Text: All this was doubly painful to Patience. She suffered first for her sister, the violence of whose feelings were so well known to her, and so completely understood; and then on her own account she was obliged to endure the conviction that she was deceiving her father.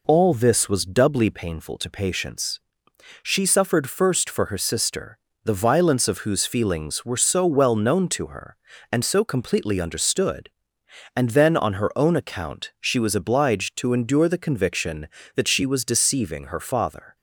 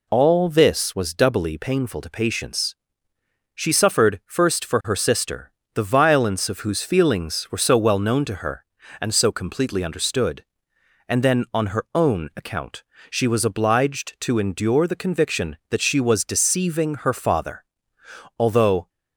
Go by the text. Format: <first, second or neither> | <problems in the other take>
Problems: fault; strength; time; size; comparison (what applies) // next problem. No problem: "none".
first | pauses between "account" and "she"; slight; at 12.8 s; 0.26 s long // goes on to say "Although"; from 18.3 s on; 0.52 s long